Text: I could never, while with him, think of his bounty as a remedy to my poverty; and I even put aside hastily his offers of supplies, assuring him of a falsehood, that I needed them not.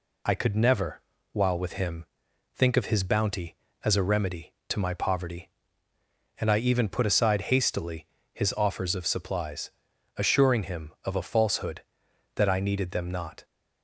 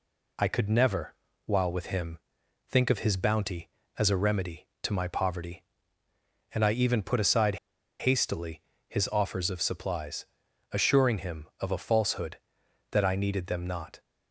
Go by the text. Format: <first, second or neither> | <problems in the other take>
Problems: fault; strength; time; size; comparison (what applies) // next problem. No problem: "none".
first | pauses between "aside" and "hastily"; at 7.5 s; 0.43 s long // pauses between "hastily" and "his"; slight; at 8.5 s; 0.28 s long; slight in the first